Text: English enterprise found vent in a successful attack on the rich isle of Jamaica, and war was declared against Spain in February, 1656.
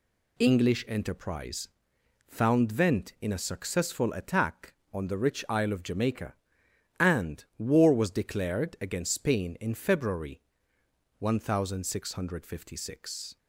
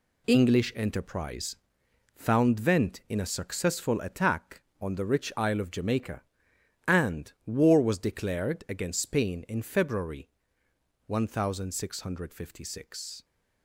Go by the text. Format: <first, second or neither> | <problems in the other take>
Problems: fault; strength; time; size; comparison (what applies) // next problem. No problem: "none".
first | gets quieter; strong; throughout; 8.5 dB // pauses between "enterprise" and "found"; noticeable; at 1.5 s; 0.60 s long; noticeable in the first